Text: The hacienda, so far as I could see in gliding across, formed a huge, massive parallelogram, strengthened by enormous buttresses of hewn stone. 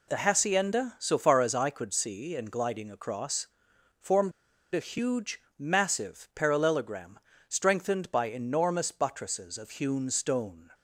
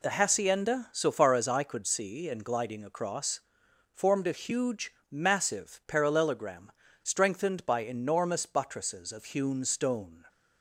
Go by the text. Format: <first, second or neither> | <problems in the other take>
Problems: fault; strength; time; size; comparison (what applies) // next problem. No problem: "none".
second | pauses between "formed" and "a"; at 4.3 s; 0.42 s long